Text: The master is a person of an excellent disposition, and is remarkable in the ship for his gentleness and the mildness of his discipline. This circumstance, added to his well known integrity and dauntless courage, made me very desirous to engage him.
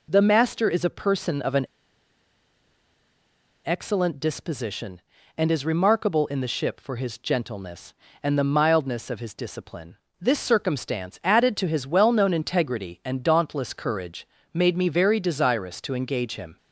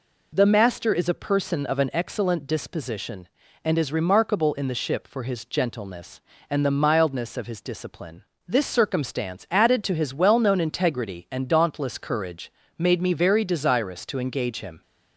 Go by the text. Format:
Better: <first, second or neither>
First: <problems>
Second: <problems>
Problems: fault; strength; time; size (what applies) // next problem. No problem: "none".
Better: second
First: pauses between "an" and "excellent"; strong; at 1.6 s; 1.9 s long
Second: none